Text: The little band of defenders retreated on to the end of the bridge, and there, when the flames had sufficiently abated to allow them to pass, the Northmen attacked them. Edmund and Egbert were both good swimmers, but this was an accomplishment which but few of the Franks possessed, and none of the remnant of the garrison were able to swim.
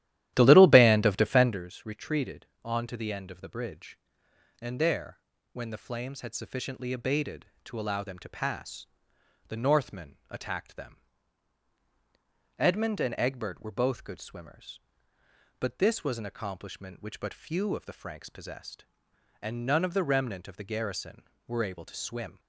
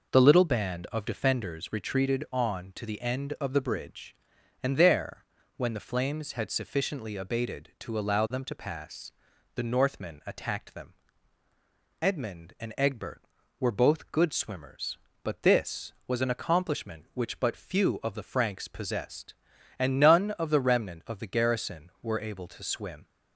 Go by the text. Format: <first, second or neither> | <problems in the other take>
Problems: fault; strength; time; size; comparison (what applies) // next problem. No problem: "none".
second | starts louder than the rest; strong; until 1.7 s; 13 dB